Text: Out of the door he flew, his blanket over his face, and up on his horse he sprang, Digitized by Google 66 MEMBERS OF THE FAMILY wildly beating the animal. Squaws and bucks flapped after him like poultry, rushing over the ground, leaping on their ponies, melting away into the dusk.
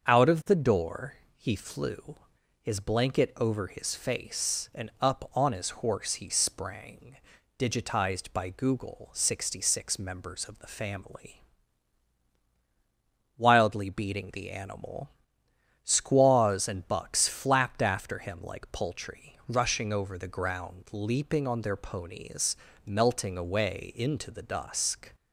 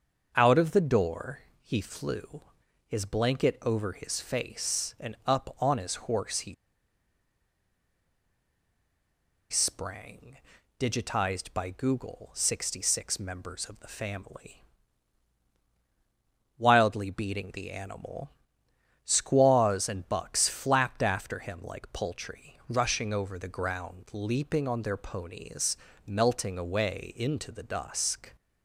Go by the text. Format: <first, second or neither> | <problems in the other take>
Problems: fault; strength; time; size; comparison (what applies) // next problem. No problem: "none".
first | starts louder than the rest; until 1.3 s; 6.5 dB; also in the first // pauses between "door" and "he"; slight; at 1.3 s; 0.22 s long; slight in the first // pauses between "he" and "sprang"; strong; at 6.5 s; 2.9 s long // pauses between "FAMILY" and "wildly"; strong; at 14.6 s; 1.9 s long; strong in the first